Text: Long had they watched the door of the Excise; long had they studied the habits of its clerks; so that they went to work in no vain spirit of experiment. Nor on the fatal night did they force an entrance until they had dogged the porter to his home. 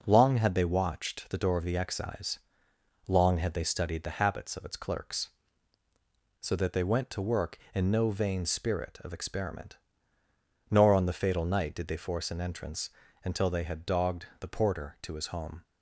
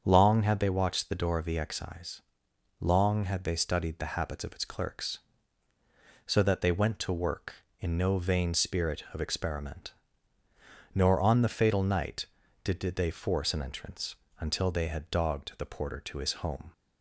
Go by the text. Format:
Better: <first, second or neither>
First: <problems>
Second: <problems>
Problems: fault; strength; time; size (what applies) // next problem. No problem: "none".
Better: first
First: pauses between "entrance" and "until"; slight; at 12.8 s; 0.34 s long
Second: starts louder than the rest; strong; until 1.0 s; 7.5 dB // says "did" twice; at 12.8 s // pauses between "entrance" and "until"; slight; at 14.1 s; 0.24 s long